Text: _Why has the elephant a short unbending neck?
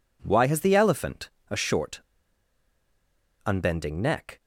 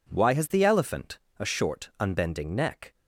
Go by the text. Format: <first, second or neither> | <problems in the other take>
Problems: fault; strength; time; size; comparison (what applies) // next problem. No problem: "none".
second | pauses between "elephant" and "a"; slight; at 1.3 s; 0.18 s long; slight in the second // pauses between "short" and "unbending"; strong; at 2.0 s; 1.4 s long